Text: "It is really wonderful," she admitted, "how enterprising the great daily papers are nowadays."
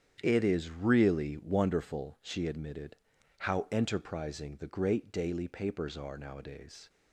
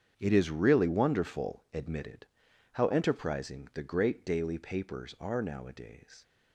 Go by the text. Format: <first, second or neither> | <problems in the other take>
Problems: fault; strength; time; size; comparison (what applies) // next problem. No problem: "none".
first | starts louder than the rest; strong; until 1.1 s; 8 dB; strong in the first // skips "she"; at 1.6 s